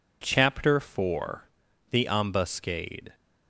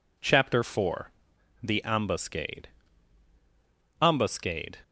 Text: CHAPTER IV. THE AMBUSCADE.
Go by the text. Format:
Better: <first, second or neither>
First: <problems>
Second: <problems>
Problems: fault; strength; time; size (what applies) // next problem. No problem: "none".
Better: first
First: none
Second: says "AMBUSCADE" twice; at 4.0 s